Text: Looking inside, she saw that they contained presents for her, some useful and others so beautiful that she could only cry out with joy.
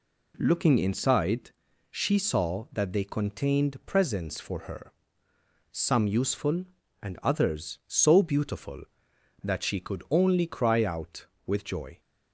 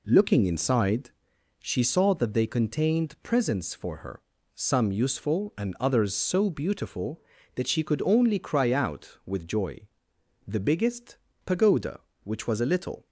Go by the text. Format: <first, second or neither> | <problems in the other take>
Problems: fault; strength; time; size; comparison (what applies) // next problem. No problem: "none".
first | goes on to say "The biggest pagoda which was a little"; strong; from 10.4 s on; 2.6 s long